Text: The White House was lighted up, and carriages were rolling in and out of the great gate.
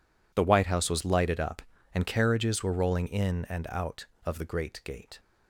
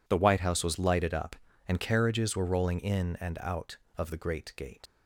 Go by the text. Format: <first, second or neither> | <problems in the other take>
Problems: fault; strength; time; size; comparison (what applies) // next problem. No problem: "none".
first | leaves "gate" unfinished; at 4.8 s; 60 ms